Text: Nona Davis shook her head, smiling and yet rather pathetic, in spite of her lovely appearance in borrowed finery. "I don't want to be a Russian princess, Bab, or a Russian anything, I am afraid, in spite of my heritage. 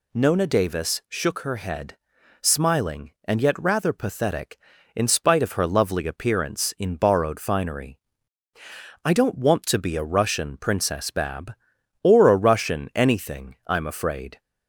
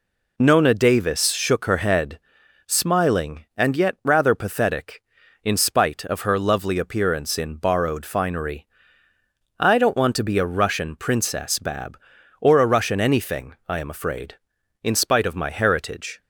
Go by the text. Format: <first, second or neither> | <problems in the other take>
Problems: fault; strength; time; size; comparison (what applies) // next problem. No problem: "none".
second | stops before "in spite of my heritage"; at 14.4 s